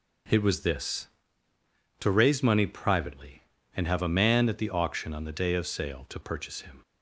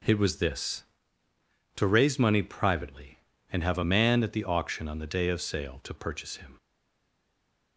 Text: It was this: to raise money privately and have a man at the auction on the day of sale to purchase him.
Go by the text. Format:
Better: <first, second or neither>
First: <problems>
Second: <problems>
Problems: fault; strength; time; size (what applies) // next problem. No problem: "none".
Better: first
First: none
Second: stays silent after the last word; noticeable; from 6.5 s on; 1.2 s long